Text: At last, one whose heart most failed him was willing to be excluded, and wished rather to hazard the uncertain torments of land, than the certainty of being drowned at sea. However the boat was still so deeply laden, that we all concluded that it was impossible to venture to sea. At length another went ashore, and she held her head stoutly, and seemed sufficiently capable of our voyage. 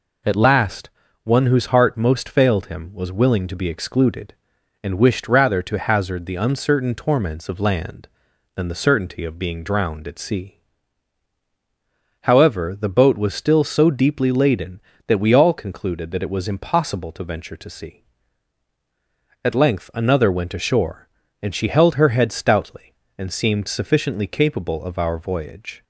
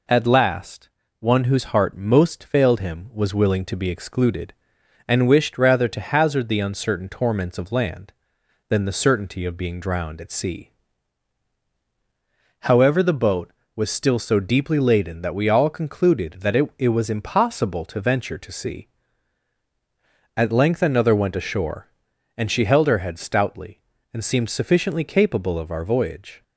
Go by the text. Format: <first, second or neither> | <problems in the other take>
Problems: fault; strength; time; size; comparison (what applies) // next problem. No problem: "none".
first | says "it" twice; at 16.7 s